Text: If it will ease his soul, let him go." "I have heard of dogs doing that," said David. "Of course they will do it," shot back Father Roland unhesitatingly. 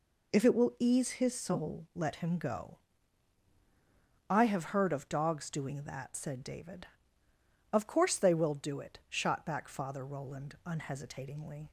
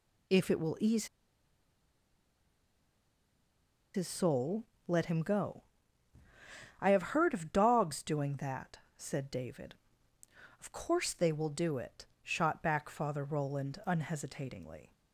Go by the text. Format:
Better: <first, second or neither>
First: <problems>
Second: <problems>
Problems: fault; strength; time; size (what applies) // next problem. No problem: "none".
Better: first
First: none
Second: pauses between "ease" and "his"; strong; at 1.0 s; 2.8 s long